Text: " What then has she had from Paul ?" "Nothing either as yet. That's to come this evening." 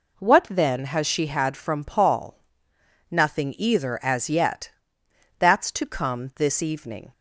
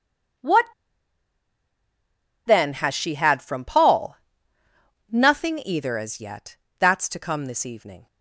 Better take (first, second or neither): first